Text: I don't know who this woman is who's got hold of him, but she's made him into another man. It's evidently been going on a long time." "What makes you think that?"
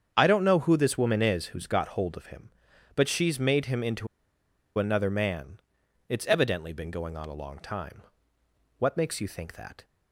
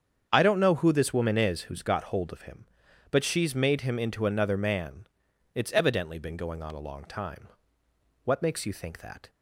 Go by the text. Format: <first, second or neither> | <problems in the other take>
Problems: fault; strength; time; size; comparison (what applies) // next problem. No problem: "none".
second | starts louder than the rest; strong; until 1.1 s; 8 dB; strong in the second // pauses between "into" and "another"; noticeable; at 4.0 s; 0.71 s long